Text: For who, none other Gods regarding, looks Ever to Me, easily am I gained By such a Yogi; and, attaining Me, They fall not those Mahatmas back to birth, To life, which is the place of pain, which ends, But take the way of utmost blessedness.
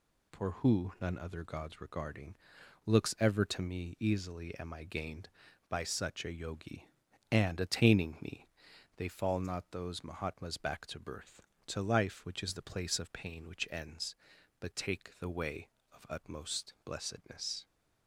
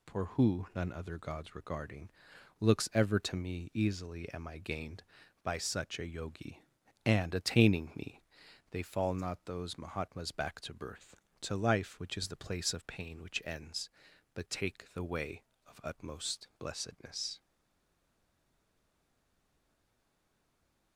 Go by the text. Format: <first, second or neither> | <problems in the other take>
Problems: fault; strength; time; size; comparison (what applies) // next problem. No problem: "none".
first | stays silent after the last word; strong; from 17.3 s on; 3.6 s long